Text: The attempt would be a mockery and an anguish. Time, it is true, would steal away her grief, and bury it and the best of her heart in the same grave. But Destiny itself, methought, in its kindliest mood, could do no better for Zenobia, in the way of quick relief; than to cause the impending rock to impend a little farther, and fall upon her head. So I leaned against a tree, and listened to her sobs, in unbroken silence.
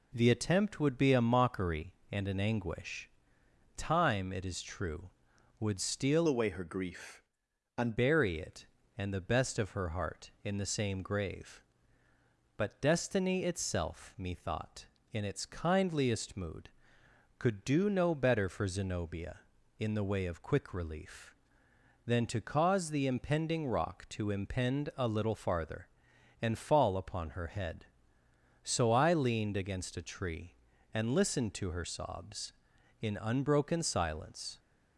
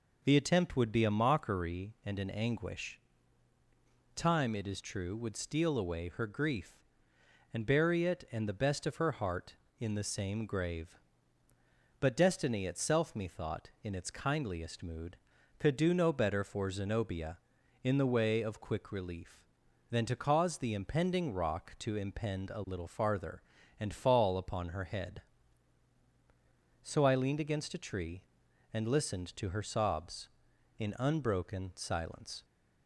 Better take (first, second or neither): second